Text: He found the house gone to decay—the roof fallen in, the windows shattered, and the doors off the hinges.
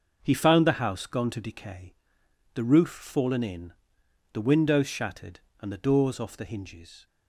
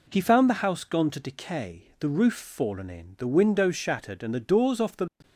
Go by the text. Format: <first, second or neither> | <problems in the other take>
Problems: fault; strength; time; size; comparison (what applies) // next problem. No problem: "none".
first | stops before "hinges"; at 5.2 s